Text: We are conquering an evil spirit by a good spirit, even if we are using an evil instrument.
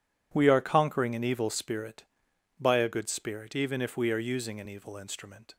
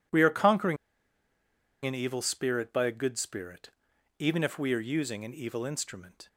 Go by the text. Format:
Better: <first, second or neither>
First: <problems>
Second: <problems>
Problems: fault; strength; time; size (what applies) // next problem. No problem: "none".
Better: first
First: none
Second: pauses between "conquering" and "an"; at 0.7 s; 1.0 s long